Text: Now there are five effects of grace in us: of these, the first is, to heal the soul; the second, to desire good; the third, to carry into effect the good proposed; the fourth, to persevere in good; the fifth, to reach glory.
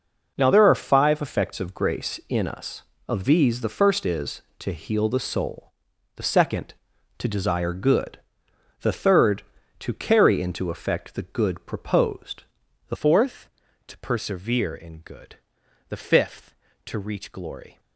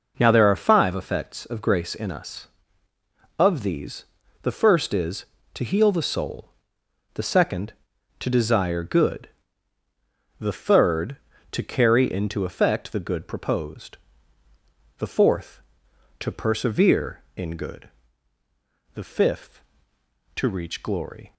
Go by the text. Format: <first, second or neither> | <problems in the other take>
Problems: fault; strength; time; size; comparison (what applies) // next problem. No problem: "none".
second | changes voice at "fourth"; from 12.9 s on; 4.8 s long